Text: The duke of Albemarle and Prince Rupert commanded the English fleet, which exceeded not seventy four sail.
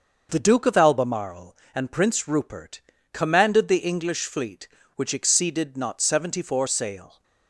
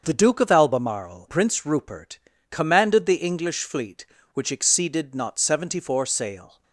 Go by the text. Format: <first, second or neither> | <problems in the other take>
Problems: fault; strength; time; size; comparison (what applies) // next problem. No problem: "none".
first | starts louder than the rest; until 1.0 s; 7 dB; also in the first // skips "and"; at 1.2 s // pauses between "Rupert" and "commanded"; slight; at 2.1 s; 0.32 s long; slight in the first